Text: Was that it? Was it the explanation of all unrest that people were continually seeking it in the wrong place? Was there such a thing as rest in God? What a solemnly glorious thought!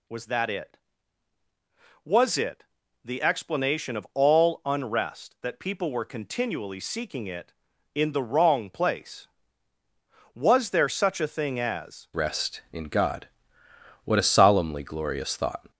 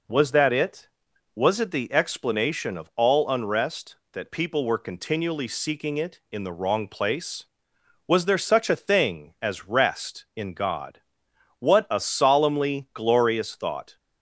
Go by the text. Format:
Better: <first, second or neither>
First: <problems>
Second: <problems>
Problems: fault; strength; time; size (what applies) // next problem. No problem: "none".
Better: second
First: pauses between "it" and "the"; at 2.6 s; 0.40 s long // changes voice at "rest"; from 12.1 s on; 3.6 s long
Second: none